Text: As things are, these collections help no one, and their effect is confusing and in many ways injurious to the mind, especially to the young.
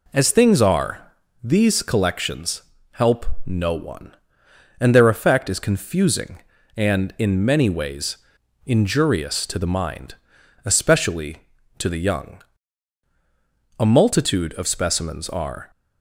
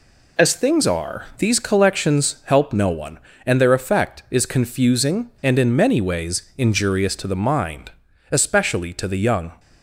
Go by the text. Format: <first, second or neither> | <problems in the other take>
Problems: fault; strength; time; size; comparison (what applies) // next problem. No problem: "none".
second | pauses between "collections" and "help"; slight; at 2.6 s; 0.30 s long // pauses between "help" and "no"; slight; at 3.2 s; 0.18 s long // pauses between "ways" and "injurious"; noticeable; at 8.1 s; 0.48 s long // goes on to say "A multitude of specimens are"; strong; from 13.7 s on; 1.9 s long